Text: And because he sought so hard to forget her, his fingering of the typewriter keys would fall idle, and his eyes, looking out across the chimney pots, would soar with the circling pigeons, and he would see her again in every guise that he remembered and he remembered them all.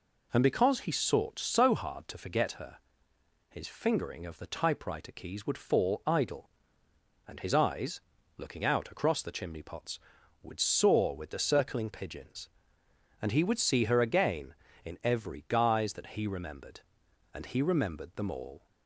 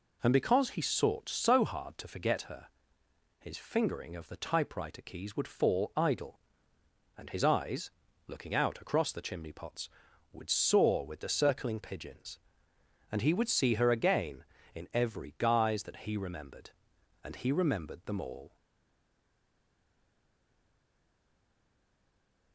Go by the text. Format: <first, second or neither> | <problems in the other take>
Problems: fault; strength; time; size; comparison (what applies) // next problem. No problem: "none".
first | stays silent after the last word; strong; from 18.5 s on; 4.0 s long